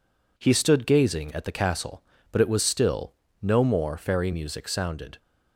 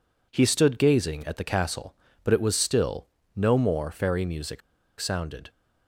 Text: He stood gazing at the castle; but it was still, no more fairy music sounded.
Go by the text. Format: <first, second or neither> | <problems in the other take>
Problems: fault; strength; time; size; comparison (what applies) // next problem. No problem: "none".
first | pauses between "music" and "sounded"; at 4.6 s; 0.39 s long